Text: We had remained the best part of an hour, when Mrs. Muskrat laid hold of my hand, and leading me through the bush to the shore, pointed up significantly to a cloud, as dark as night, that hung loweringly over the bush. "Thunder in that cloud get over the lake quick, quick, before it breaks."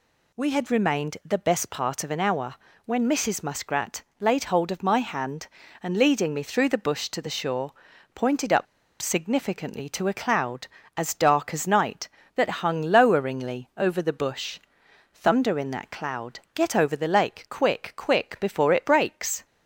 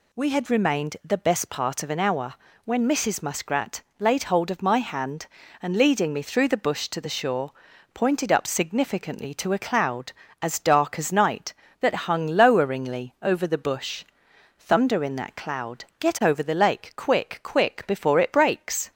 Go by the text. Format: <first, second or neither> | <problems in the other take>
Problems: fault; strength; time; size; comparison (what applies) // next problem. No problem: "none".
second | pauses between "Muskrat" and "laid"; slight; at 4.0 s; 0.18 s long; slight in the second // pauses between "up" and "significantly"; slight; at 8.6 s; 0.35 s long